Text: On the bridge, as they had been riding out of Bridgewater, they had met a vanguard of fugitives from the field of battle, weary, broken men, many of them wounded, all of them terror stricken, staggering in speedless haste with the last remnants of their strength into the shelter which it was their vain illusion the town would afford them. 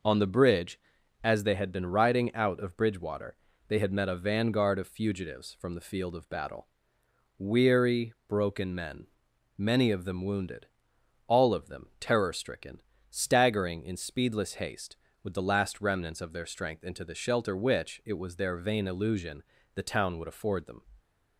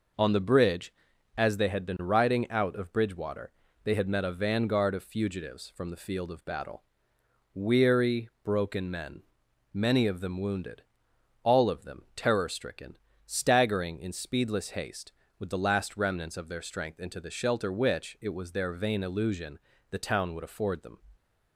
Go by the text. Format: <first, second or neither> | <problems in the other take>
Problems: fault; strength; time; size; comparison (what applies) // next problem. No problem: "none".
neither | pauses between "illusion" and "the"; slight; the same in both